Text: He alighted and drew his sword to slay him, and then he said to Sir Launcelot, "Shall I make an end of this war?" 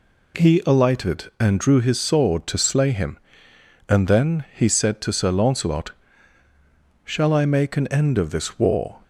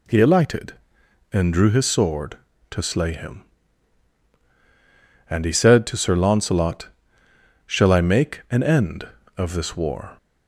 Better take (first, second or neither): first